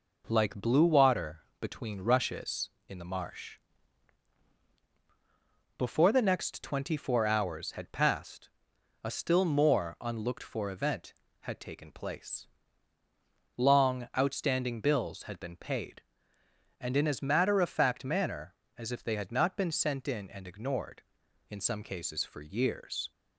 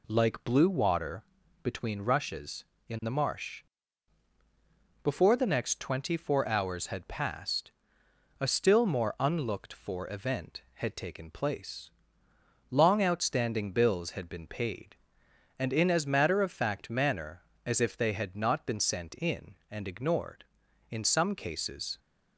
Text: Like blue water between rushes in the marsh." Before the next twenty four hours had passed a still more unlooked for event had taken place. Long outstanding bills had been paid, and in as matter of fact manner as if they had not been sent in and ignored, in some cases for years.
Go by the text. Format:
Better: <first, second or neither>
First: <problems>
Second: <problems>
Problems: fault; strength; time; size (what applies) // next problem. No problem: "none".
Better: first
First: pauses between "water" and "between"; slight; at 1.4 s; 0.18 s long // pauses between "passed" and "a"; noticeable; at 8.4 s; 0.54 s long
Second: pauses between "water" and "between"; at 1.2 s; 0.40 s long // pauses between "passed" and "a"; noticeable; at 7.7 s; 0.68 s long // stops before "for years"; at 21.9 s